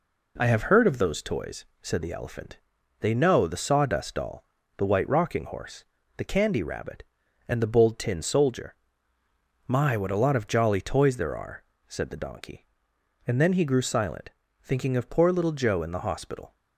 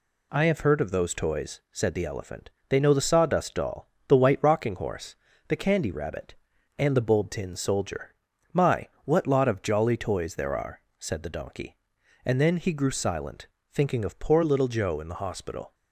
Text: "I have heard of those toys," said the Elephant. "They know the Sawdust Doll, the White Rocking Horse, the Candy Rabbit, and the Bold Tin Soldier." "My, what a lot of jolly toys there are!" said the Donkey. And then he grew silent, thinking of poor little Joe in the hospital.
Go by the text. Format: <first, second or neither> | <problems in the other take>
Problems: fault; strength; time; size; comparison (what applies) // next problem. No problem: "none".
first | skips "a"; at 9.2 s